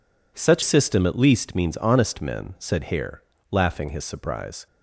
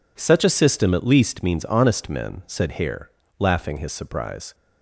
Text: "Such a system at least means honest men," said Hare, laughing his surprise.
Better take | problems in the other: second | skips "a"; at 0.6 s

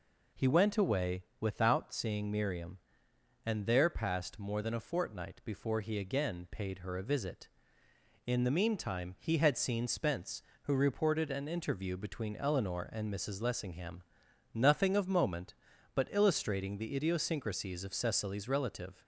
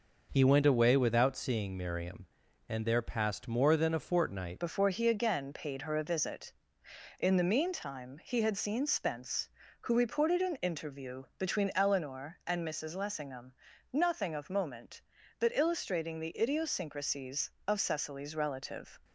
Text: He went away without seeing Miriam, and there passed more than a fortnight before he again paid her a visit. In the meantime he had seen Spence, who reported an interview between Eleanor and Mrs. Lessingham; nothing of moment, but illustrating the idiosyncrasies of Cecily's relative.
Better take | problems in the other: first | changes voice at "before"; from 4.5 s on; 14.4 s long

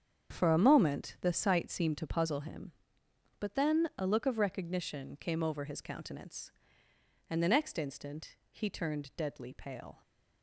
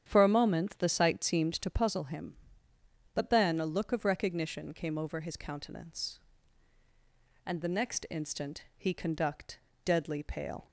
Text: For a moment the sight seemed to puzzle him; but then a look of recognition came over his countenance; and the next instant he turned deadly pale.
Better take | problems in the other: first | starts louder than the rest; strong; until 1.0 s; 9 dB; strong in the first // says "conduct" for "turned"; at 8.9 s

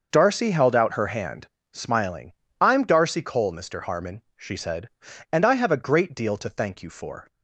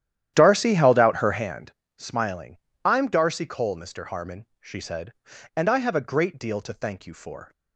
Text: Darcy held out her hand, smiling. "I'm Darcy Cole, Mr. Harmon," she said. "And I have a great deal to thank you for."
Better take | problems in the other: first | starts louder than the rest; strong; until 1.5 s; 11 dB

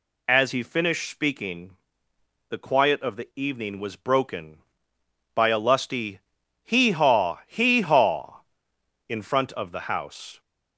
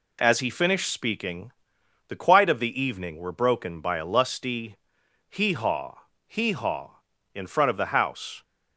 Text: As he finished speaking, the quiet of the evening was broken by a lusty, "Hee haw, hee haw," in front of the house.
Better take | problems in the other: first | says "were" for "was"; at 3.1 s

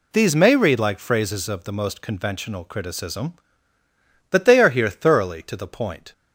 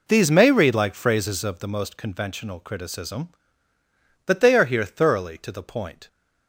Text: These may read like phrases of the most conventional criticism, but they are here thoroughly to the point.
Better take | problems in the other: first | starts louder than the rest; until 1.9 s; 3.5 dB

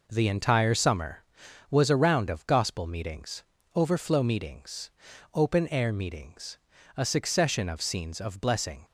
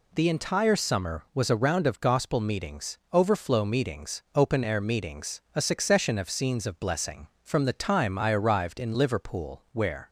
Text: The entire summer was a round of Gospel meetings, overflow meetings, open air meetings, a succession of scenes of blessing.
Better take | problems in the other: first | goes on to say "From the time I arrived in Liverpool where"; strong; from 7.4 s on; 2.6 s long

